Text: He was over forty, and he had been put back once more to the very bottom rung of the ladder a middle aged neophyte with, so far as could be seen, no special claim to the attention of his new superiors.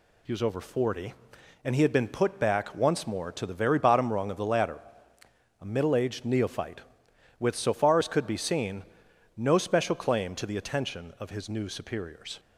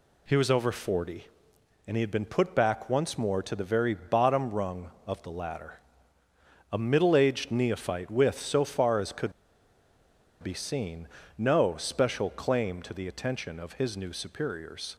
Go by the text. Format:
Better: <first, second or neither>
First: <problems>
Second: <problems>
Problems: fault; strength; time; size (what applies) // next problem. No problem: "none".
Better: first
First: pauses between "ladder" and "a"; noticeable; at 4.8 s; 0.80 s long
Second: pauses between "ladder" and "a"; noticeable; at 5.7 s; 0.94 s long // pauses between "could" and "be"; at 9.3 s; 1.0 s long